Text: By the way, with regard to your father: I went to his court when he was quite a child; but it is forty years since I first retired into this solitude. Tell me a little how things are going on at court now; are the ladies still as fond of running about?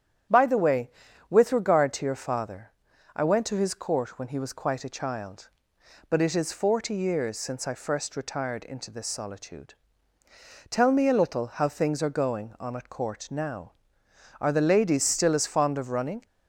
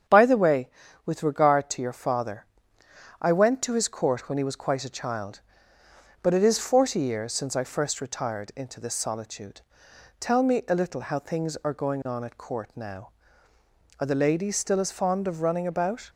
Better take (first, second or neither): second